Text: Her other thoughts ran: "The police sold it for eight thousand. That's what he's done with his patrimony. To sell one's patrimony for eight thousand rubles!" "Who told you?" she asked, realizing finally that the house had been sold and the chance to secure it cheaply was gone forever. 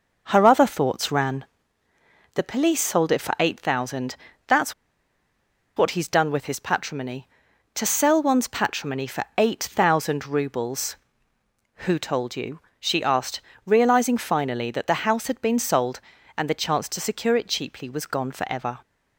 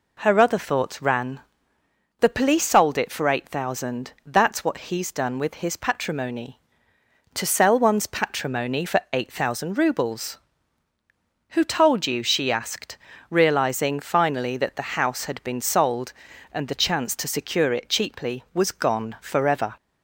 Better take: second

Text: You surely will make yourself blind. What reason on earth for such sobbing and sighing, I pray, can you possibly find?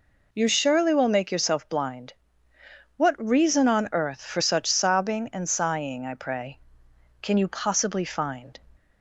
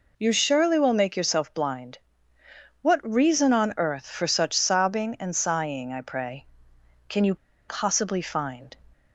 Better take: first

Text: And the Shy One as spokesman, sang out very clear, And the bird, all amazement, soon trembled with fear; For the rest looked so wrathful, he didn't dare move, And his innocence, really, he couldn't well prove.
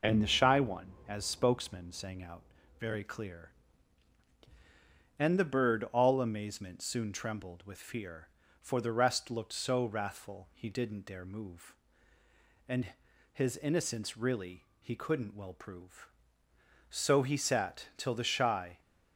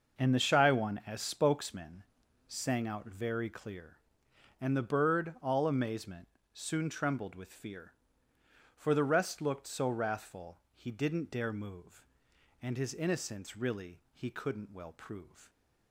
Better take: second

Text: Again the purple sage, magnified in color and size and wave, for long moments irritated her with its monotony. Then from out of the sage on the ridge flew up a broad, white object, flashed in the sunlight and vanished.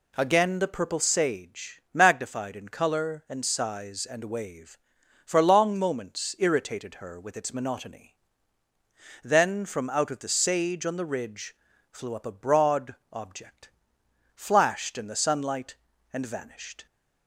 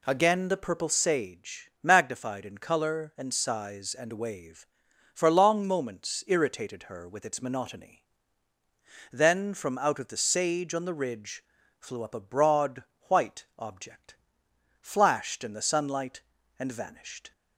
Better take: second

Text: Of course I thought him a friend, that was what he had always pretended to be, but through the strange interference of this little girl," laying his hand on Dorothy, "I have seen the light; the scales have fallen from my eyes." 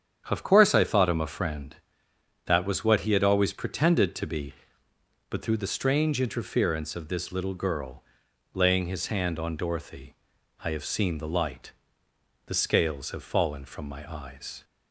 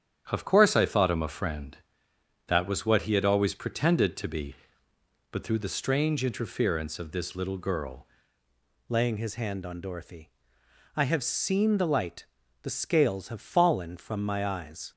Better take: first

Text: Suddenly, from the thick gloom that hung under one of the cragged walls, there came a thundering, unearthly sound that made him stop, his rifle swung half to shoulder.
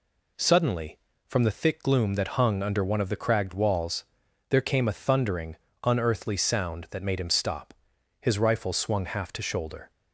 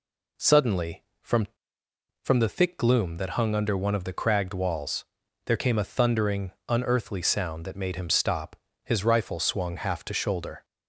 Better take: first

